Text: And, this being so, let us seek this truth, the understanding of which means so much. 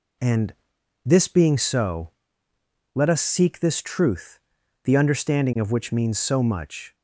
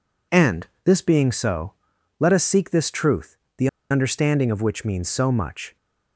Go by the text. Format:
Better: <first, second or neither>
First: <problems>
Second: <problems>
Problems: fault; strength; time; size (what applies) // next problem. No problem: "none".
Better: first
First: none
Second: pauses between "the" and "understanding"; slight; at 3.6 s; 0.21 s long